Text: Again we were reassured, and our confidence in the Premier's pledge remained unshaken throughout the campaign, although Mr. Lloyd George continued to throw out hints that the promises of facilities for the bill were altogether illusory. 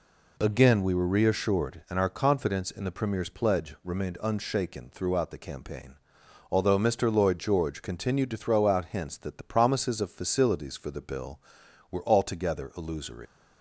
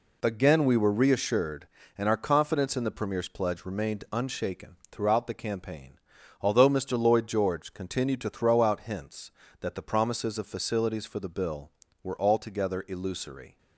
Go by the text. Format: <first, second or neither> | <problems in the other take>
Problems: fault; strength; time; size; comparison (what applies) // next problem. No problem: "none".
second | leaves "illusory" unfinished; at 13.2 s; 115 ms